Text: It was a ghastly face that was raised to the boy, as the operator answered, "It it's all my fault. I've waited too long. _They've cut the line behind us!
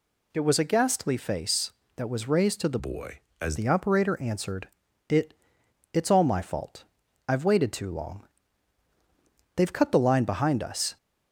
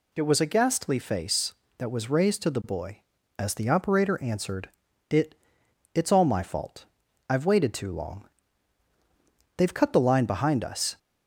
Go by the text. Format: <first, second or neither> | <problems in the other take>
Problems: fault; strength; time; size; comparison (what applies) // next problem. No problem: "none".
second | changes voice from "boy" to "as"; from 2.7 to 3.5 s; 0.8 s long // pauses between "It" and "it's"; noticeable; at 5.3 s; 0.58 s long; noticeable in the second